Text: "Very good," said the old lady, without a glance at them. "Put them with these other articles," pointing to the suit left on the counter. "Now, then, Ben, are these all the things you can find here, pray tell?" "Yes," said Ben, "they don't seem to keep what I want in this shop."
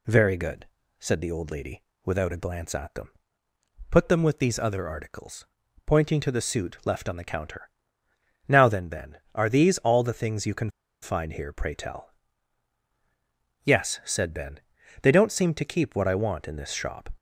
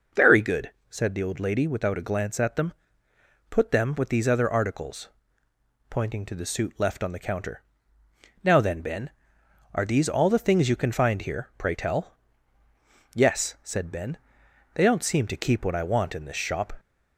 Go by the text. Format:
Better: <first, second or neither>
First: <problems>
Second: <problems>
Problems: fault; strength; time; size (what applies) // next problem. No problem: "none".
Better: second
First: pauses between "can" and "find"; slight; at 10.7 s; 0.31 s long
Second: none